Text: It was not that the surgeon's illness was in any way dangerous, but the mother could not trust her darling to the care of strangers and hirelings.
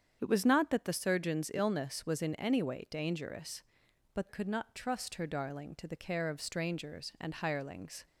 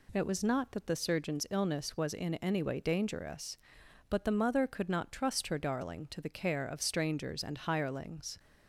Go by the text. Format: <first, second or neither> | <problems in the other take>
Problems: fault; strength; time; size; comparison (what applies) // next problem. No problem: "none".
second | starts louder than the rest; strong; until 1.2 s; 8 dB // skips "the mother"; at 4.2 s